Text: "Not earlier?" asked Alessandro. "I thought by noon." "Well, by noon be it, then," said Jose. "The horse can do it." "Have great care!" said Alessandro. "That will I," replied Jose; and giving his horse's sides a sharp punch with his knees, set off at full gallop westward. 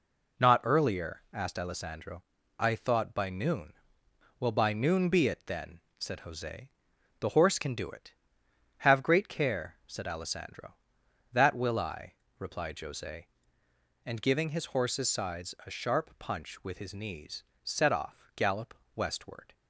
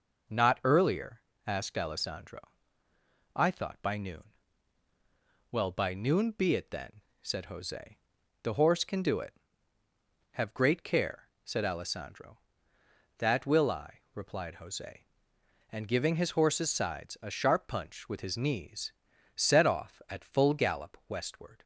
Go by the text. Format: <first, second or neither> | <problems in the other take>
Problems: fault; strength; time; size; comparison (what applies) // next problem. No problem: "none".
second | skips "at full"; at 18.3 s // pauses between "gallop" and "westward"; slight; at 18.7 s; 0.20 s long